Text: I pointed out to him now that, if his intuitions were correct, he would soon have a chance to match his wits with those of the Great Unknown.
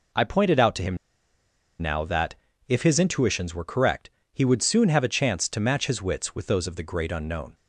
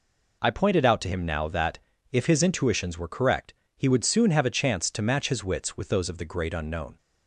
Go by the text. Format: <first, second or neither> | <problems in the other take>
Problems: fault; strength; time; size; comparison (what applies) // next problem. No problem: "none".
second | pauses between "him" and "now"; noticeable; at 0.9 s; 0.83 s long